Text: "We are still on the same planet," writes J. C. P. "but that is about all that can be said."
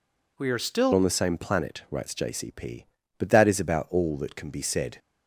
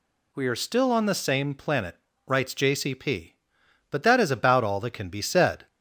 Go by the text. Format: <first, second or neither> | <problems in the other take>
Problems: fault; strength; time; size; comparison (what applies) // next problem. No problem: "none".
second | changes voice at "on"; from 0.9 s on; 4.0 s long